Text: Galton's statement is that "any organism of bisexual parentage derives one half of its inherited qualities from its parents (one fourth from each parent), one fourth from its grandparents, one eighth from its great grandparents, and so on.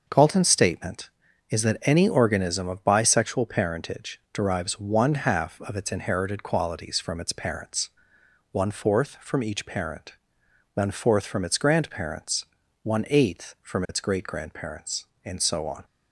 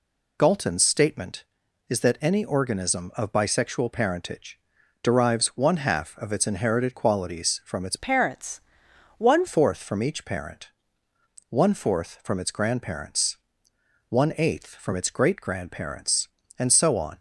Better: first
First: none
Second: pauses between "parentage" and "derives"; at 4.5 s; 0.44 s long // changes voice from "parents" to "one"; from 7.9 to 9.4 s; 1.5 s long

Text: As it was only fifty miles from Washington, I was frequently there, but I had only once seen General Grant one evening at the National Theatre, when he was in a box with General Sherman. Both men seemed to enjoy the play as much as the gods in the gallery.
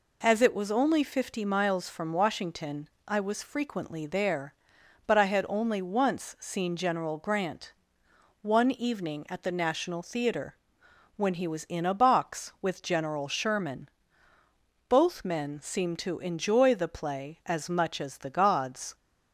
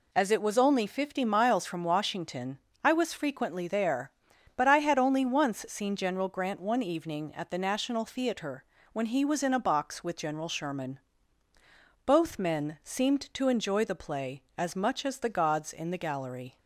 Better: second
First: pauses between "Grant" and "one"; noticeable; at 7.7 s; 0.68 s long // stops before "in the gallery"; at 18.9 s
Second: none

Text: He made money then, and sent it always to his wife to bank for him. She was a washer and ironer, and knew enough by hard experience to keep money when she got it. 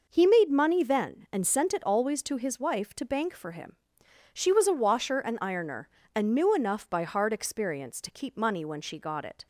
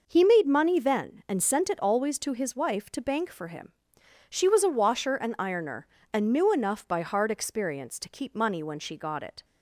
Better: neither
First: none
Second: none

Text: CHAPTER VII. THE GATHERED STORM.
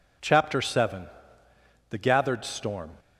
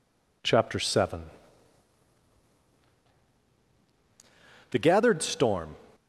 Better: neither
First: none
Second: none

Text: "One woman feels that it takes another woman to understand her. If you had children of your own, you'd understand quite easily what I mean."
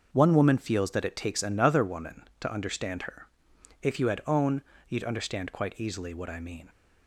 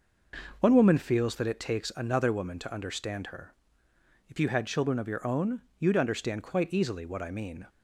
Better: second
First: starts louder than the rest; until 1.1 s; 6.5 dB // skips "children of your"; at 4.2 s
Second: none

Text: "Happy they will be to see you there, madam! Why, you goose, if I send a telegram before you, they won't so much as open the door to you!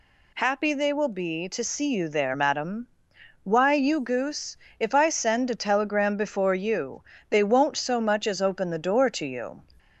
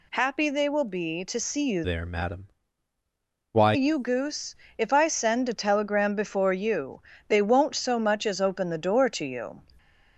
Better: first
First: none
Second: changes voice from "there" to "Why"; from 1.8 to 3.7 s; 1.9 s long

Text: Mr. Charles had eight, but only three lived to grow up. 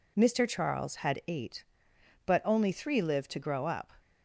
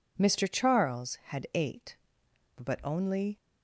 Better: first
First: none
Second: stops before "three lived to grow up"; at 3.3 s

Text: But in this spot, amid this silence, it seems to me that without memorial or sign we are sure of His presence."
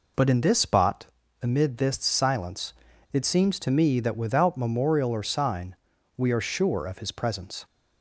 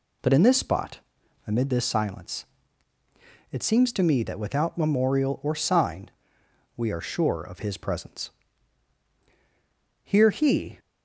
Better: first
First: pauses between "sign" and "we"; at 5.7 s; 0.42 s long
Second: pauses between "sign" and "we"; noticeable; at 6.1 s; 0.66 s long // goes on to say "Here he"; noticeable; from 10.0 s on; 0.76 s long

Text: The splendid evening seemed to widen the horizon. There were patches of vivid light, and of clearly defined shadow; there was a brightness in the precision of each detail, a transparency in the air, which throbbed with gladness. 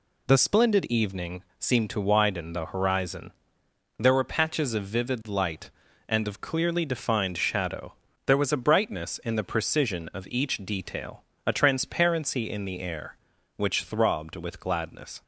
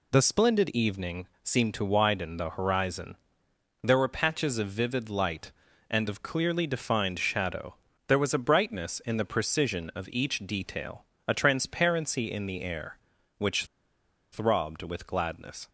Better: first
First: pauses between "evening" and "seemed"; slight; at 1.4 s; 0.16 s long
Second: pauses between "evening" and "seemed"; slight; at 1.2 s; 0.16 s long // pauses between "which" and "throbbed"; noticeable; at 13.6 s; 0.68 s long

